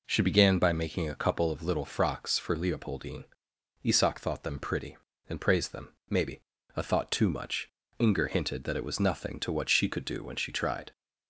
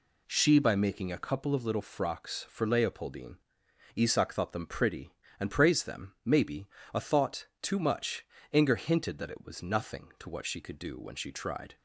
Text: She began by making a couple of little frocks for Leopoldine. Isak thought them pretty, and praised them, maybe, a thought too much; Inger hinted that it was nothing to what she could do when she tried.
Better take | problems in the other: first | skips "began"; at 0.5 s // pauses between "thought" and "too"; slight; at 7.4 s; 0.16 s long

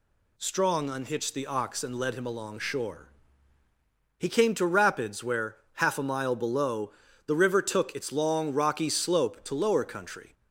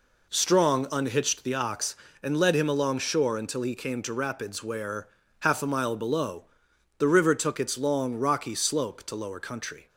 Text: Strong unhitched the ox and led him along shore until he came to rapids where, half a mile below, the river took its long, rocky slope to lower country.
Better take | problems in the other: second | skips "until"; at 3.6 s

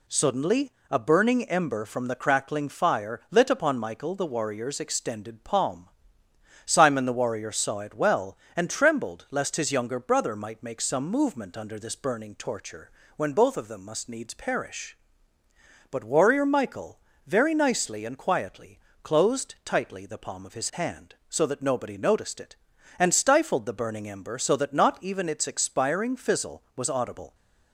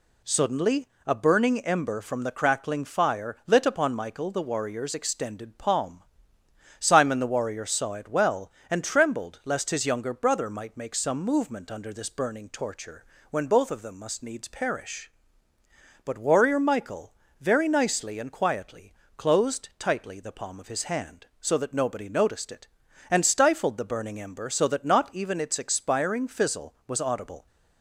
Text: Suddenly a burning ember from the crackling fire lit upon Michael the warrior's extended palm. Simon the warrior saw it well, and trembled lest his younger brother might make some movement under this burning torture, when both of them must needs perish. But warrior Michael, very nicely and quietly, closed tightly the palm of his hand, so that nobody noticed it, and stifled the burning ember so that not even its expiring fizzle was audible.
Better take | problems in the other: neither | pauses between "Suddenly" and "a"; slight; the same in both

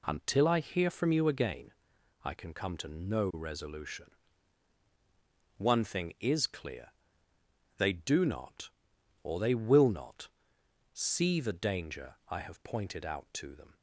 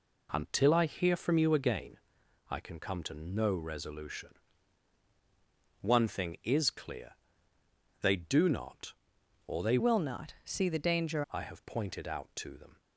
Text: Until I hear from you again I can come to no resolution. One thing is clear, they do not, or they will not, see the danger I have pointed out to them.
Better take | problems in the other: first | pauses between "again" and "I"; noticeable; at 1.9 s; 0.54 s long; noticeable in the first // changes voice from "will" to "danger"; from 9.7 to 11.2 s; 1.5 s long

